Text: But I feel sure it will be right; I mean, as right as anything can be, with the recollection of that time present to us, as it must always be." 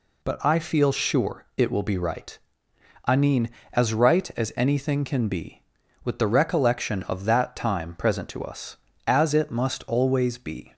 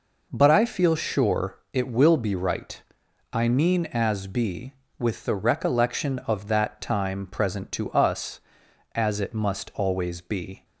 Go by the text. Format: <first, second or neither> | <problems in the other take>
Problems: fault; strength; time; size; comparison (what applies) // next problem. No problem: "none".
first | pauses between "sure" and "it"; slight; at 1.5 s; 0.16 s long // skips "right as anything can"; at 4.2 s